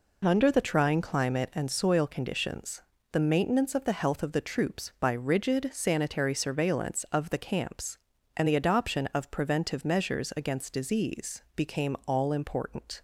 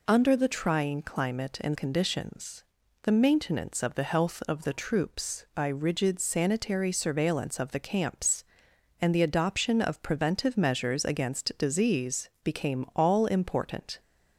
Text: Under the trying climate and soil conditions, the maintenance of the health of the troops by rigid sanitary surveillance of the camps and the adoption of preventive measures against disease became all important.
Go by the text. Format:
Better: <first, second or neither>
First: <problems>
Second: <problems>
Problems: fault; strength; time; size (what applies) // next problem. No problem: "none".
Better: first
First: none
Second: skips "soil"; at 1.7 s // pauses between "disease" and "became"; slight; at 12.2 s; 0.16 s long